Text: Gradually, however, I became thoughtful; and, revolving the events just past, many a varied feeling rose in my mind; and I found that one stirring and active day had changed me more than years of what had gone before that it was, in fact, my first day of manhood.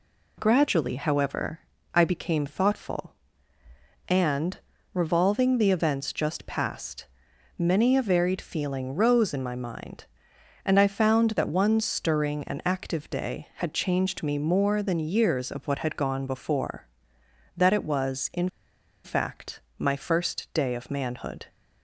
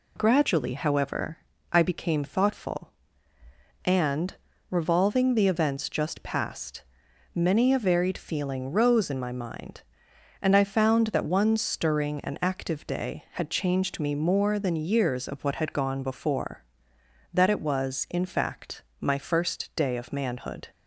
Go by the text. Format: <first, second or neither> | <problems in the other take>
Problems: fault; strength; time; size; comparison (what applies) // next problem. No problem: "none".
second | pauses between "in" and "fact"; noticeable; at 18.4 s; 0.57 s long